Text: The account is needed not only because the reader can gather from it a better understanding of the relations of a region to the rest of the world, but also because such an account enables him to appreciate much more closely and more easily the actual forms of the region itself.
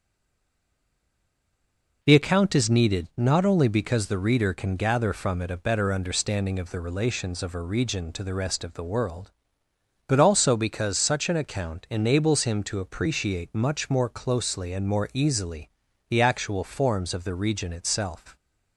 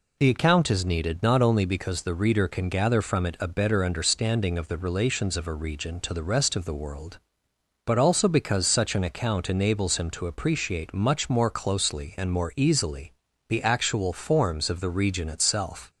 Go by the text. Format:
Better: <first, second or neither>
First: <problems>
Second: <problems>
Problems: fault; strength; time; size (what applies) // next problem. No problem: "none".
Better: second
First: stays silent before the first word; noticeable; until 2.0 s; 2.0 s long // pauses between "easily" and "the"; at 15.6 s; 0.40 s long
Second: pauses between "easily" and "the"; at 13.1 s; 0.38 s long